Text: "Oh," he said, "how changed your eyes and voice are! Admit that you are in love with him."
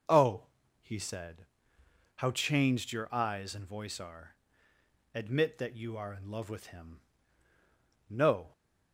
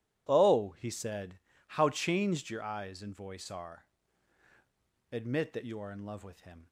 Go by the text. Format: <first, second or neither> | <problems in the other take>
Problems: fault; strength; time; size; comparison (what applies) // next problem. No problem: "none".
second | goes on to say "No"; slight; from 8.0 s on; 0.44 s long